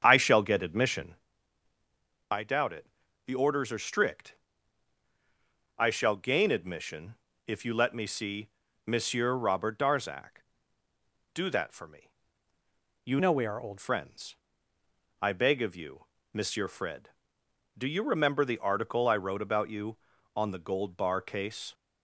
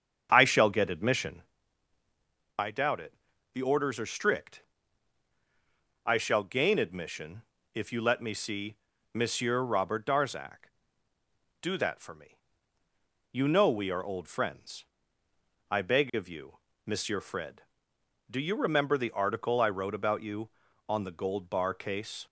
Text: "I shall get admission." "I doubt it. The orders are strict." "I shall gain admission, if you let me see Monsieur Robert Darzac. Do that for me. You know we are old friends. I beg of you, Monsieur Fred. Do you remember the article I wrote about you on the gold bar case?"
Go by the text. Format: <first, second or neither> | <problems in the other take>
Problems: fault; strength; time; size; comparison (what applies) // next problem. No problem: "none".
second | starts louder than the rest; strong; until 1.0 s; 8 dB; strong in the second // pauses between "see" and "Monsieur"; slight; at 8.4 s; 0.36 s long; slight in the second // changes voice from "know" to "old"; from 13.1 to 13.7 s; 0.6 s long